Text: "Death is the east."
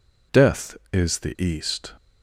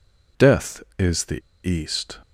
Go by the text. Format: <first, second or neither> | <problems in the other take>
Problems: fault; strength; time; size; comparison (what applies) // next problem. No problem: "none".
first | pauses between "the" and "east"; slight; at 1.4 s; 0.25 s long